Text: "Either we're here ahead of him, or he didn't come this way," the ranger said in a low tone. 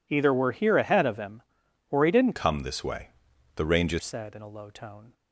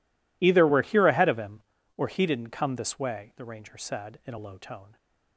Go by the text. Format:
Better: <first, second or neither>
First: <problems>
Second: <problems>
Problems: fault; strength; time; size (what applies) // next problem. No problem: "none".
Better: second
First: changes voice from "come" to "ranger"; from 2.3 to 3.9 s; 1.6 s long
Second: none